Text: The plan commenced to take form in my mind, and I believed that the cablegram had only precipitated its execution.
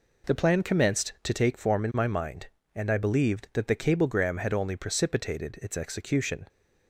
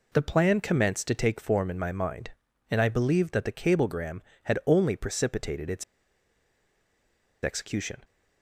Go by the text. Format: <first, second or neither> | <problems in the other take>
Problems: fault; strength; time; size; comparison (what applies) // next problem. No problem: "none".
first | pauses between "its" and "execution"; strong; at 5.8 s; 1.6 s long